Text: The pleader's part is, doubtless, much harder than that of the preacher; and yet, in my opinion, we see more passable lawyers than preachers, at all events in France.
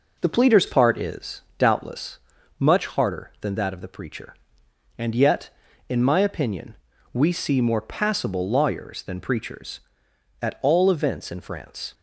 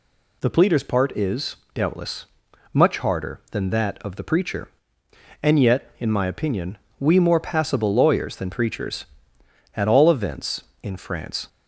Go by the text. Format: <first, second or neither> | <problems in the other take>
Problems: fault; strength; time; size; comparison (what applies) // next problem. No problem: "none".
first | skips "see"; at 7.1 s